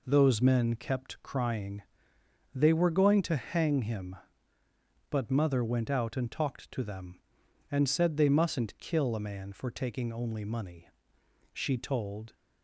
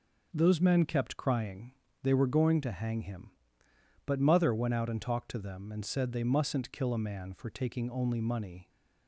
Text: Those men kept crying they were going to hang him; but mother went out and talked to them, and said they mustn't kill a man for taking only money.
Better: second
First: pauses between "crying" and "they"; noticeable; at 1.8 s; 0.74 s long // goes on to say "She told"; noticeable; from 11.5 s on; 0.82 s long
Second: pauses between "crying" and "they"; slight; at 1.7 s; 0.30 s long

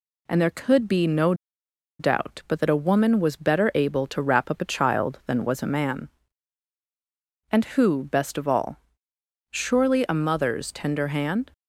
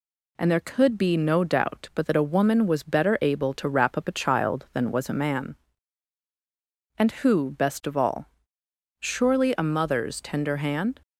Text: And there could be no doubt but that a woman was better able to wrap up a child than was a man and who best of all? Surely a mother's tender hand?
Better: second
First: pauses between "no" and "doubt"; noticeable; at 1.3 s; 0.66 s long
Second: none

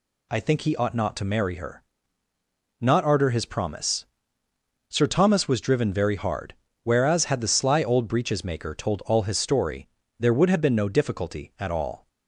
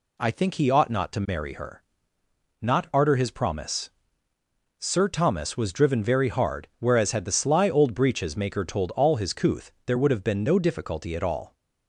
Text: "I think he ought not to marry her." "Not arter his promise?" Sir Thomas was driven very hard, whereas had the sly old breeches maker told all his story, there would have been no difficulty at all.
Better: first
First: none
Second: says "couth" for "story"; at 9.3 s

